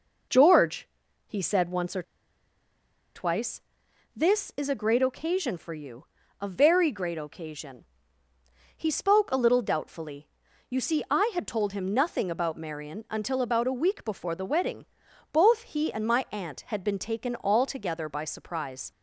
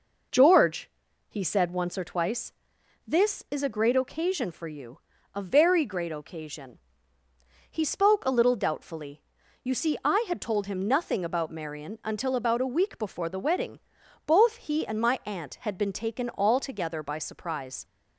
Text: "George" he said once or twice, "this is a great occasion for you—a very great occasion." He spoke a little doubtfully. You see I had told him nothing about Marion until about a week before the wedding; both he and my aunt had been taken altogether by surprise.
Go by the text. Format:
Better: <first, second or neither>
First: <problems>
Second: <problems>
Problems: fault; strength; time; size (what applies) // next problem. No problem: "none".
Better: second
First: pauses between "George" and "he"; at 0.8 s; 0.40 s long // pauses between "or" and "twice"; at 2.0 s; 1.1 s long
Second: pauses between "George" and "he"; at 0.8 s; 0.40 s long